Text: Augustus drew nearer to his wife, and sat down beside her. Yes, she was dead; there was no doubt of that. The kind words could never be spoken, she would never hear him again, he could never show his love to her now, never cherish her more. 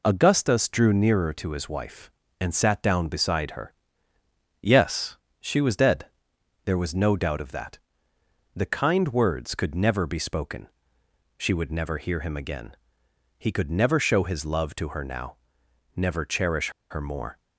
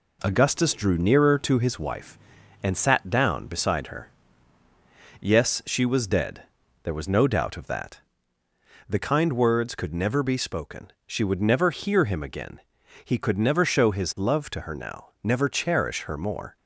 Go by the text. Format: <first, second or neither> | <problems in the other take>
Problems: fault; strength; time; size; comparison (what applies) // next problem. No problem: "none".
second | pauses between "cherish" and "her"; slight; at 16.6 s; 0.20 s long